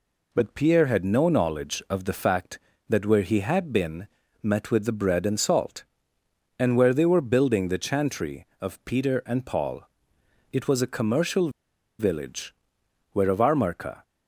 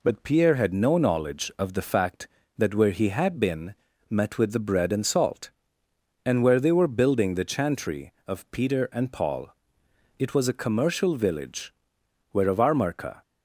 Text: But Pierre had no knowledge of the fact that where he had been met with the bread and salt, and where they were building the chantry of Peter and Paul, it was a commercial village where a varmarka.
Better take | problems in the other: second | pauses between "been" and "met"; slight; at 4.0 s; 0.34 s long; slight in the second // pauses between "commercial" and "village"; noticeable; at 11.4 s; 0.49 s long // pauses between "village" and "where"; noticeable; at 12.5 s; 0.60 s long; noticeable in the second

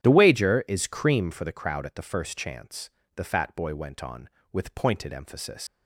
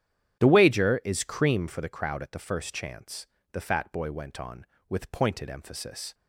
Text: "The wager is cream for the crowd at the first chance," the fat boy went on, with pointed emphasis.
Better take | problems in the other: second | starts louder than the rest; strong; until 1.0 s; 10 dB; strong in the second // leaves "emphasis" unfinished; at 5.6 s; 105 ms

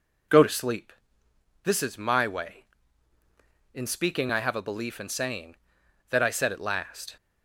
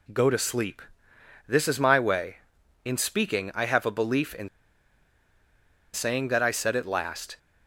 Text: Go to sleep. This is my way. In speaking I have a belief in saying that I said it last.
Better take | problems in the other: first | pauses between "in" and "saying"; strong; at 4.4 s; 1.4 s long

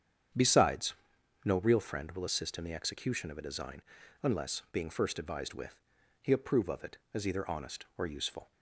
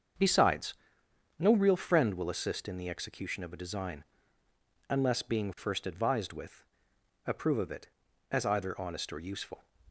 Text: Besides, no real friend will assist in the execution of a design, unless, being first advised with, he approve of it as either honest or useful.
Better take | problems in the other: first | starts louder than the rest; until 1.8 s; 7 dB; strong in the first // skips "he"; at 6.9 s

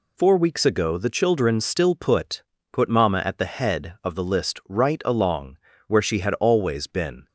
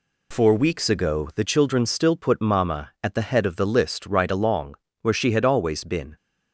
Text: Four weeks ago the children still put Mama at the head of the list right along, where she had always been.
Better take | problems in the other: second | says "put" twice; at 2.7 s

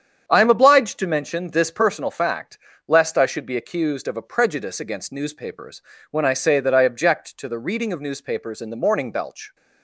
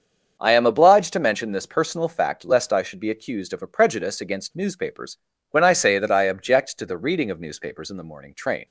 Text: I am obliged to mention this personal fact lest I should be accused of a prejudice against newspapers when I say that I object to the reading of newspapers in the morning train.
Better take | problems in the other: second | starts louder than the rest; strong; until 1.2 s; 8.5 dB; also in the second // pauses between "fact" and "lest"; slight; at 2.5 s; 0.30 s long // pauses between "newspapers" and "when"; slight; at 5.8 s; 0.26 s long; slight in the second // says "belch" for "train"; at 9.1 s

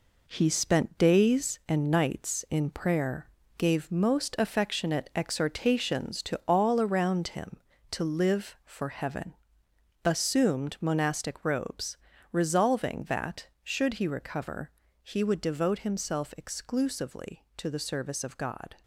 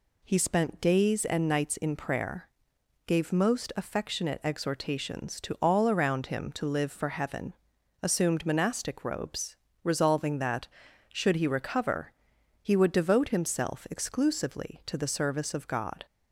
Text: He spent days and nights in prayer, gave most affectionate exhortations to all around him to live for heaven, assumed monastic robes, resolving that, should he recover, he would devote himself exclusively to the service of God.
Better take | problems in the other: second | gets quieter; throughout; 6.5 dB

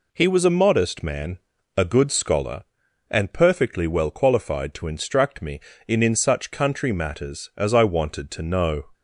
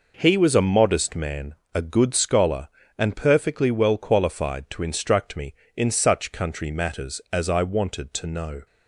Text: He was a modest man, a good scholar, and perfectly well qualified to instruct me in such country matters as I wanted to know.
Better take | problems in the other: second | says "in" twice; at 6.0 s

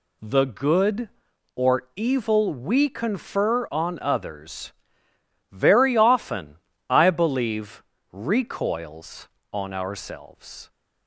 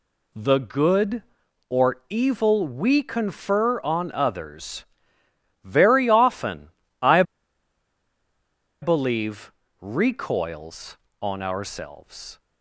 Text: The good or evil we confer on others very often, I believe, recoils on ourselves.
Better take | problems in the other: first | pauses between "others" and "very"; noticeable; at 4.8 s; 0.80 s long; noticeable in the first // pauses between "I" and "believe"; strong; at 7.2 s; 1.5 s long

